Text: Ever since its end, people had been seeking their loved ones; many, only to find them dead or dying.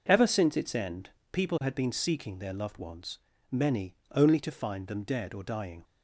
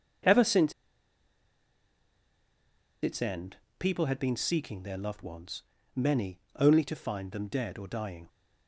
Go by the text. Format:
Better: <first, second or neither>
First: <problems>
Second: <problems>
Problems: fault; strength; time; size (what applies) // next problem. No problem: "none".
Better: first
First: none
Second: pauses between "since" and "its"; strong; at 0.7 s; 2.3 s long